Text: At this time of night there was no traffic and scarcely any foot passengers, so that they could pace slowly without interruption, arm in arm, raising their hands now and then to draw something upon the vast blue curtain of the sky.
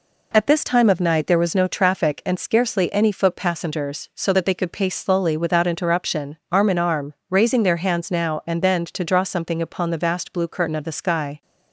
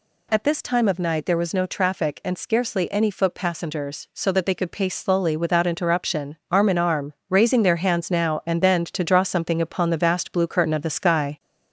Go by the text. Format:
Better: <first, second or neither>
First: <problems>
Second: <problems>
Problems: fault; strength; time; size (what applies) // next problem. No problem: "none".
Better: first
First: none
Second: gets louder; throughout; 3.5 dB